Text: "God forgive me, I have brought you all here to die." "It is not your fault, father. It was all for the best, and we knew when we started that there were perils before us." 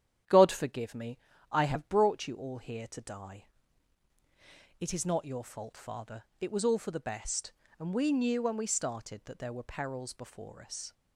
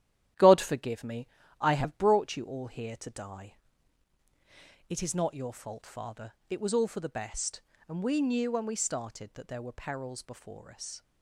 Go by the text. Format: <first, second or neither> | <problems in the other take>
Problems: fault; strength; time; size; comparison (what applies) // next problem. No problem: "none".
first | gets quieter; noticeable; throughout; 5.5 dB // starts louder than the rest; strong; until 1.6 s; 11.5 dB; strong in the first